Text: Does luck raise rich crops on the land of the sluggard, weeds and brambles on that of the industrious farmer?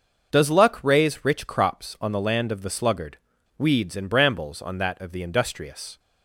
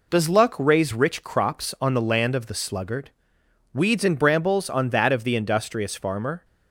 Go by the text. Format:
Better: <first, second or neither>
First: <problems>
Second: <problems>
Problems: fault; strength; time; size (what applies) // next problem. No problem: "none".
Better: second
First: starts louder than the rest; until 1.3 s; 6.5 dB // stops before "farmer"; at 5.9 s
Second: none